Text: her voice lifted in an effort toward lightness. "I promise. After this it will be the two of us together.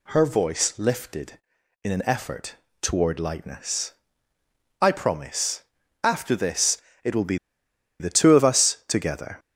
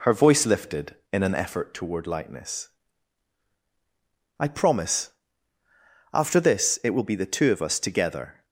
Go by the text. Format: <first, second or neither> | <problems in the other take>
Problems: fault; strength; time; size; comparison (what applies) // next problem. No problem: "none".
second | pauses between "effort" and "toward"; slight; at 2.5 s; 0.26 s long // pauses between "this" and "it"; slight; at 6.7 s; 0.26 s long // pauses between "be" and "the"; noticeable; at 7.3 s; 0.62 s long